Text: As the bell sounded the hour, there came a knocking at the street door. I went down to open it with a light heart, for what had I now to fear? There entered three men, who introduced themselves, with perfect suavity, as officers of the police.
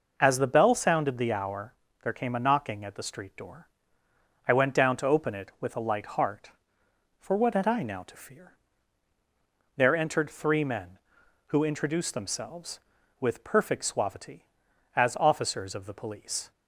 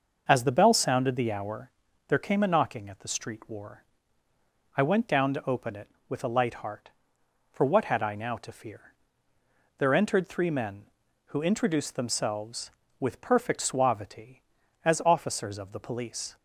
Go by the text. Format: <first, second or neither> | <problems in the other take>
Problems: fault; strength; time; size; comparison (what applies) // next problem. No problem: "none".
first | starts louder than the rest; noticeable; until 1.2 s; 6 dB // says "war" for "door"; at 3.4 s